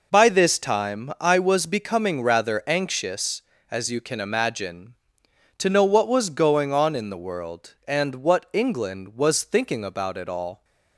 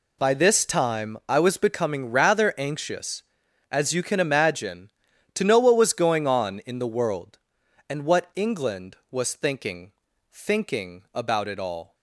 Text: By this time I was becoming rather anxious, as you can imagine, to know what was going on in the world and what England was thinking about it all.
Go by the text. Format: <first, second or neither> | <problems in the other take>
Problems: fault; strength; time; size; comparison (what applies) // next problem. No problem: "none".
first | says "thinking" twice; at 10.3 s